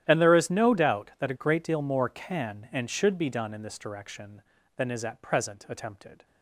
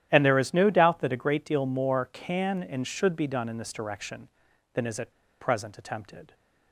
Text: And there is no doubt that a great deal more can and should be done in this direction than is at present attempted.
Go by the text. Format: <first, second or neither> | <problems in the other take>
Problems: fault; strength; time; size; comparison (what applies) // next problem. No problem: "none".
first | starts louder than the rest; strong; until 1.1 s; 11.5 dB; strong in the first // pauses between "at" and "present"; slight; at 5.1 s; 0.29 s long